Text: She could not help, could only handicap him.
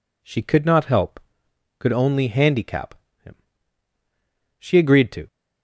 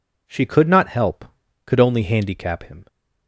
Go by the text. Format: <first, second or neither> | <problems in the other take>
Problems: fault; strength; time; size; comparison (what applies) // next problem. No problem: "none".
second | pauses between "handicap" and "him"; slight; at 2.9 s; 0.30 s long // goes on to say "She agreed to"; noticeable; from 4.5 s on; 0.70 s long